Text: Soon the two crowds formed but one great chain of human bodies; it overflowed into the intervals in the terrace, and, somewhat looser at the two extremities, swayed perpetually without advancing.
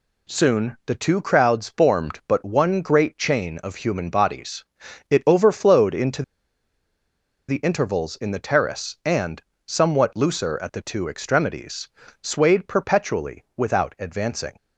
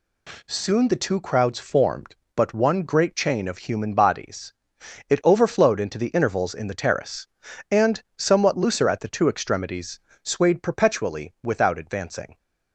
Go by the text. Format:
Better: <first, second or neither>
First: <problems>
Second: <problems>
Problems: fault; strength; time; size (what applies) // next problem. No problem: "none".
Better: second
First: pauses between "into" and "the"; strong; at 6.2 s; 1.2 s long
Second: none